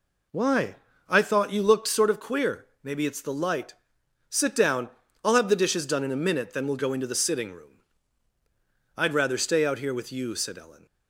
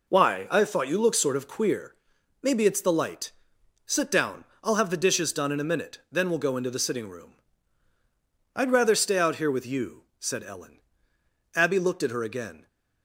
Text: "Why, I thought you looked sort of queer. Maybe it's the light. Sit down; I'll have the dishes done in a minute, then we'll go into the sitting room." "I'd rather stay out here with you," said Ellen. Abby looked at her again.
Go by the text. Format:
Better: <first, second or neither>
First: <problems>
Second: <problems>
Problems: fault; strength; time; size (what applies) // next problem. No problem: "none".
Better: second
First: stops before "Abby looked at her again"; at 10.8 s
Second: none